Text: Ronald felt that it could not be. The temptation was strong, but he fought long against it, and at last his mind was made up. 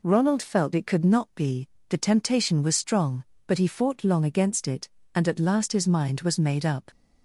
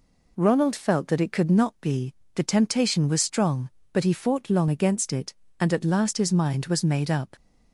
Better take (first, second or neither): second